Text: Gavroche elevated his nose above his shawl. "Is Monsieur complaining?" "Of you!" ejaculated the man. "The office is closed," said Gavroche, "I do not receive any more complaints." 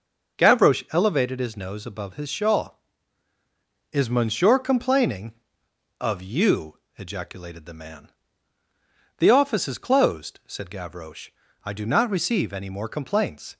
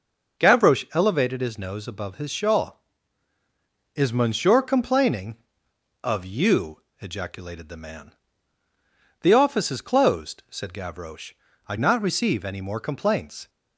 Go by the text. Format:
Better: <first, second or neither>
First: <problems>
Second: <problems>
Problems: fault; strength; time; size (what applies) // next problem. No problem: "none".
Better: first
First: starts louder than the rest; until 1.4 s; 6.5 dB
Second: starts louder than the rest; noticeable; until 1.4 s; 6 dB // skips "do"; at 11.7 s